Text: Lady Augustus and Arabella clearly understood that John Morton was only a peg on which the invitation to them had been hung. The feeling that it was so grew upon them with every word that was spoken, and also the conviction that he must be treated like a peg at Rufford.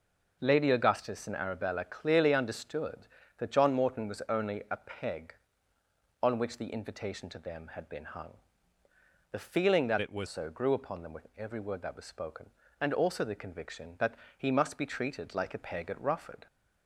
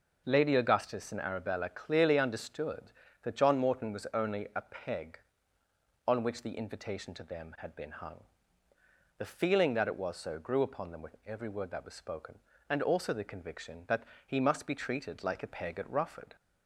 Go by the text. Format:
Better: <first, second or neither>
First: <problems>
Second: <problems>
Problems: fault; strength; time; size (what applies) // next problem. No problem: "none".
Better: second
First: changes voice from "it" to "was"; from 9.9 to 10.2 s; 0.3 s long // pauses between "that" and "he"; slight; at 14.1 s; 0.24 s long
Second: pauses between "that" and "he"; slight; at 14.0 s; 0.24 s long